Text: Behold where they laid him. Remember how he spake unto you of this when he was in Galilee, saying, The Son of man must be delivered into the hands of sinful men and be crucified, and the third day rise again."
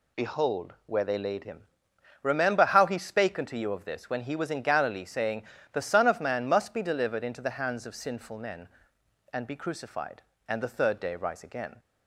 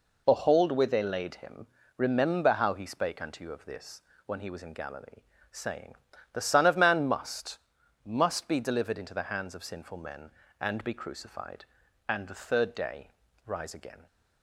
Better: first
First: none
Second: pauses between "this" and "when"; slight; at 4.0 s; 0.24 s long // says "must" twice; at 8.0 s // pauses between "day" and "rise"; at 13.0 s; 0.38 s long

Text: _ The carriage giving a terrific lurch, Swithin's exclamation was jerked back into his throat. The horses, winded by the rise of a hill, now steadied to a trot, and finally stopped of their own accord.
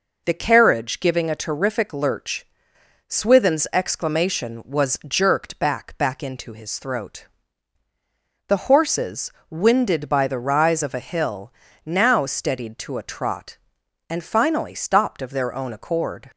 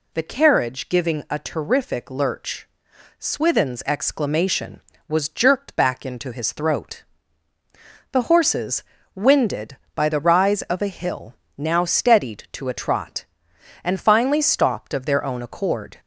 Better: second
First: says "back" twice; at 5.9 s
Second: none

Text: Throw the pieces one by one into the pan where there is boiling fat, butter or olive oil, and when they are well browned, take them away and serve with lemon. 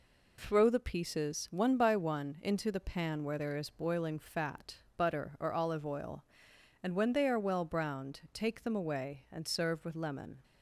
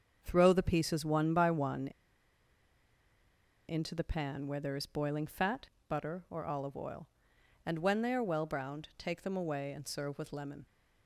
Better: first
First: none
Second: starts louder than the rest; until 1.2 s; 7 dB // pauses between "one" and "into"; strong; at 1.8 s; 1.8 s long

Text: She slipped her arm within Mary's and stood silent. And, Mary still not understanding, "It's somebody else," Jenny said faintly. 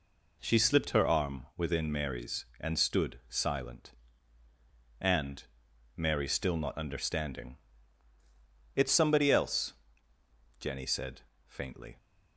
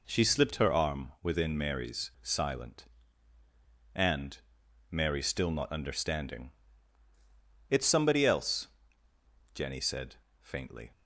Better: first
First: pauses between "said" and "faintly"; slight; at 11.2 s; 0.22 s long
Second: skips "and stood"; at 2.1 s // pauses between "said" and "faintly"; slight; at 10.1 s; 0.22 s long

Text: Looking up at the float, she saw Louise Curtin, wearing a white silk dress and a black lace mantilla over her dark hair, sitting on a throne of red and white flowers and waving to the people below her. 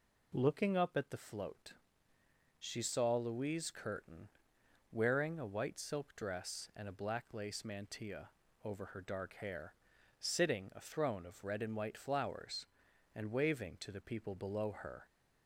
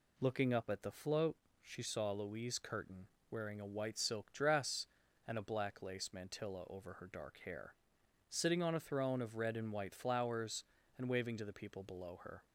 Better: second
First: pauses between "mantilla" and "over"; slight; at 8.2 s; 0.34 s long // skips "on"; at 10.7 s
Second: none

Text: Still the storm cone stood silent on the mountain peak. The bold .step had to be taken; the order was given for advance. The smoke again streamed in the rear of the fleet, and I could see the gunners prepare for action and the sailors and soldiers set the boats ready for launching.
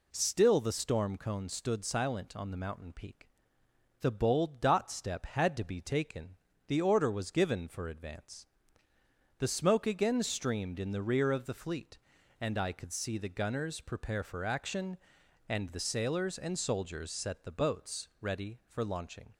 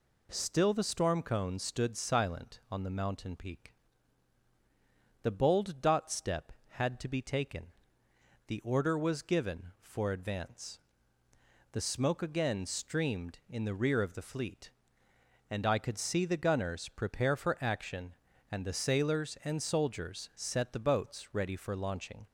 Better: neither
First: none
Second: none

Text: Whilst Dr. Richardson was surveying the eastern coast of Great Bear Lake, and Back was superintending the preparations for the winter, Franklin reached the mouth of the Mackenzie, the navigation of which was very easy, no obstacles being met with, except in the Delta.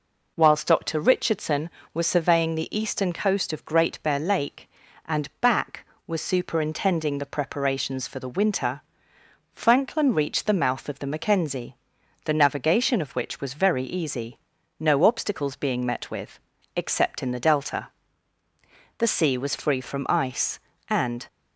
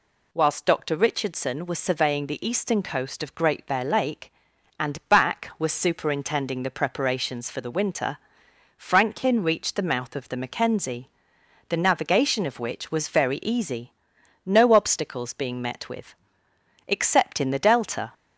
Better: second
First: goes on to say "The sea was free from ice and"; strong; from 18.9 s on; 2.2 s long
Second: none

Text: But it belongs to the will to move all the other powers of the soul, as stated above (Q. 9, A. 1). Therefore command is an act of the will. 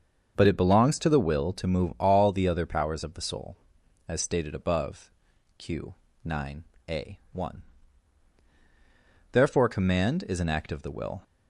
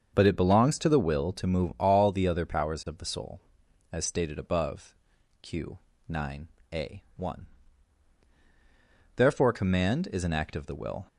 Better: neither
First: starts louder than the rest; until 1.3 s; 6.5 dB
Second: starts louder than the rest; until 1.1 s; 6.5 dB

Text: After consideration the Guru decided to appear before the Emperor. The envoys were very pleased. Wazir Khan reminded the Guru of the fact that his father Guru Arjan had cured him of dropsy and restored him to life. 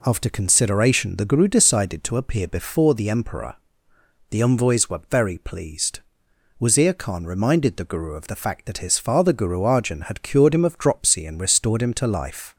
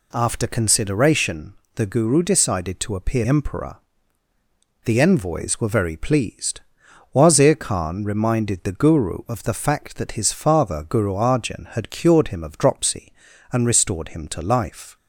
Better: first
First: none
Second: pauses between "consideration" and "the"; slight; at 1.5 s; 0.22 s long // skips "before the"; at 3.2 s

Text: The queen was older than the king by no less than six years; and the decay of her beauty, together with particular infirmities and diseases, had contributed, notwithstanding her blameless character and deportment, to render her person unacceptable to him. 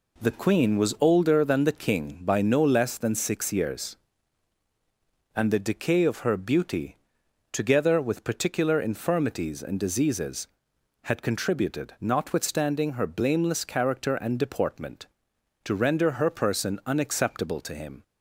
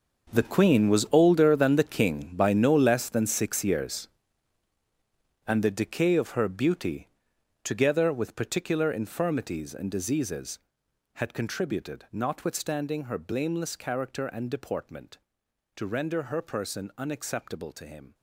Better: first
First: none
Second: gets quieter; strong; throughout; 14 dB

